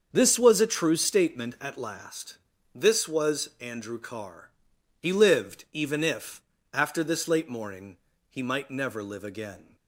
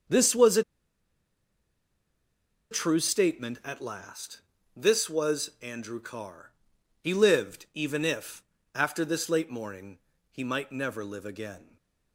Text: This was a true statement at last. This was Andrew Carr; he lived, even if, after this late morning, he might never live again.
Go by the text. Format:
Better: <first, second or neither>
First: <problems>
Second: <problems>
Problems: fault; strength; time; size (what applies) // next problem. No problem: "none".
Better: first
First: starts louder than the rest; until 1.1 s; 6.5 dB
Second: starts louder than the rest; until 3.1 s; 6.5 dB // pauses between "a" and "true"; strong; at 0.6 s; 2.0 s long // stays silent after the last word; slight; from 11.6 s on; 0.5 s long